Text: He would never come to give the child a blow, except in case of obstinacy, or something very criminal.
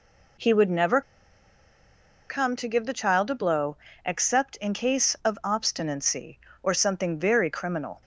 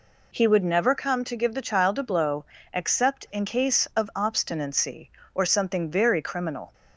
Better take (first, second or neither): second